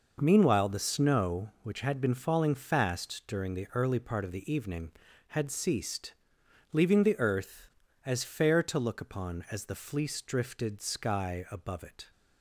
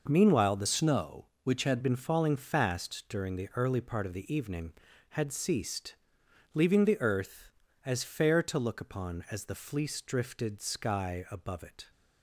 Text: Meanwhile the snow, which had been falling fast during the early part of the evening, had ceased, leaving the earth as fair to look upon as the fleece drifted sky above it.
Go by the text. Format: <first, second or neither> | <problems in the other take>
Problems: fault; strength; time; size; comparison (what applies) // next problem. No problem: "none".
first | changes voice from "snow" to "had"; from 0.6 to 1.7 s; 1.1 s long